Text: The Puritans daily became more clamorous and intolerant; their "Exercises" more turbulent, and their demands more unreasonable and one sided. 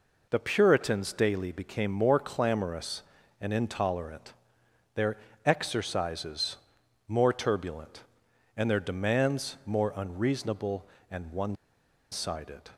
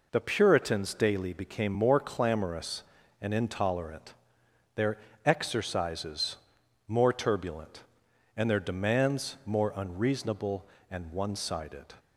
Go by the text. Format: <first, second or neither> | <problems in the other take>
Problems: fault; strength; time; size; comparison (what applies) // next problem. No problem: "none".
second | pauses between "their" and "Exercises"; slight; at 5.1 s; 0.28 s long; slight in the second // pauses between "Exercises" and "more"; noticeable; at 6.5 s; 0.50 s long; noticeable in the second // pauses between "one" and "sided"; noticeable; at 11.5 s; 0.57 s long